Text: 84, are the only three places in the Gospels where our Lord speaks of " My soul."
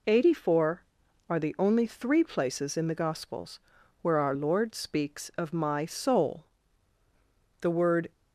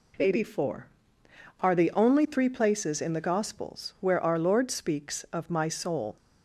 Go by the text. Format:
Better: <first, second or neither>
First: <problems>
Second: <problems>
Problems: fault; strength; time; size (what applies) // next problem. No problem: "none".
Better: second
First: pauses between "Gospels" and "where"; at 3.6 s; 0.42 s long // goes on to say "The word"; from 7.5 s on; 0.52 s long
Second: none